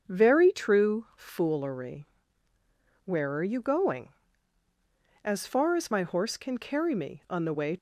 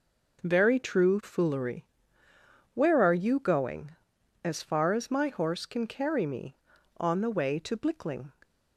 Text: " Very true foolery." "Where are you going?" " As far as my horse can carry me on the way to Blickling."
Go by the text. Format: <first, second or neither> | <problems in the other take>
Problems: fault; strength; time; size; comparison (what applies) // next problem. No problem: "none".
second | starts louder than the rest; strong; until 1.0 s; 7.5 dB // stops before "to Blickling"; at 7.7 s